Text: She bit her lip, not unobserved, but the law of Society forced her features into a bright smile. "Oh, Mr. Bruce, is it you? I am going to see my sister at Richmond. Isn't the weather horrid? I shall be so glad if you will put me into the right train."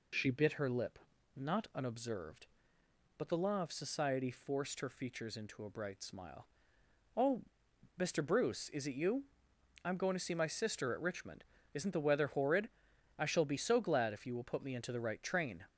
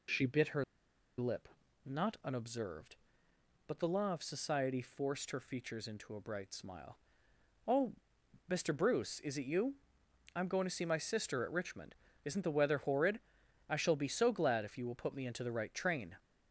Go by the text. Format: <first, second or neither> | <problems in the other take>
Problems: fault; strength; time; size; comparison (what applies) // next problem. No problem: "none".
first | pauses between "her" and "lip"; noticeable; at 0.6 s; 0.55 s long